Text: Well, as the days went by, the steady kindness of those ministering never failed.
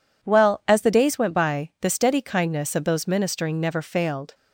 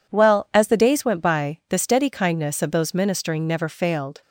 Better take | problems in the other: neither | none

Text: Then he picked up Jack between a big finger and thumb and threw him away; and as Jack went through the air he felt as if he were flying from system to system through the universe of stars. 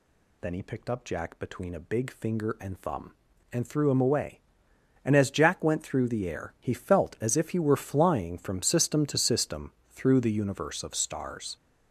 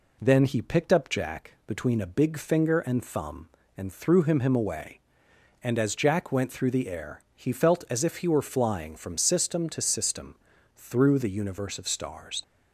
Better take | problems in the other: first | says "him" twice; at 4.4 s // pauses between "system" and "through"; at 10.3 s; 0.40 s long; slight in the first

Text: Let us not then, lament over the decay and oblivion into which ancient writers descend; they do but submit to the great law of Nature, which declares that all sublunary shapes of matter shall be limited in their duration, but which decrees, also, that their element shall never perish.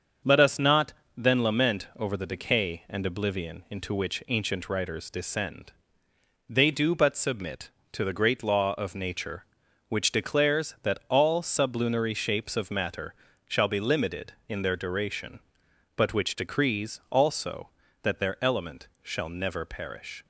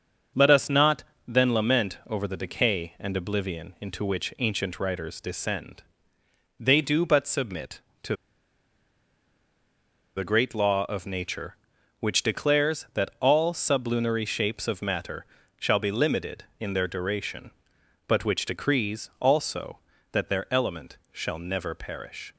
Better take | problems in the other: first | starts louder than the rest; until 1.5 s; 6.5 dB; also in the first // pauses between "not" and "then"; slight; at 1.0 s; 0.22 s long; slight in the first // pauses between "to" and "the"; strong; at 8.1 s; 2.0 s long // pauses between "matter" and "shall"; slight; at 15.2 s; 0.32 s long; slight in the first // pauses between "element" and "shall"; slight; at 20.9 s; 0.16 s long; slight in the first

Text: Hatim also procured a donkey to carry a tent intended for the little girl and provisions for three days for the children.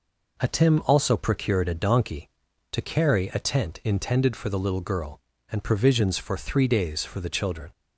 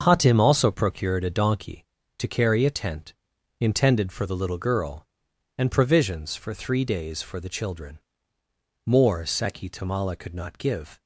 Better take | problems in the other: first | starts louder than the rest; until 1.0 s; 6.5 dB // pauses between "tent" and "intended"; noticeable; at 3.1 s; 0.46 s long // goes on to say "More Seki Tamala could not give"; strong; from 8.8 s on; 2.1 s long

